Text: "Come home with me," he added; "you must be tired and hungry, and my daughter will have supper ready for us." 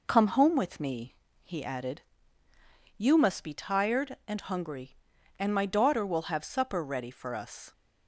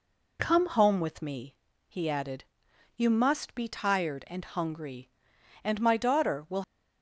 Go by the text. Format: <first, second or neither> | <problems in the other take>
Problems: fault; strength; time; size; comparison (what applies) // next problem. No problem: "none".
first | stops before "have supper ready for us"; at 6.6 s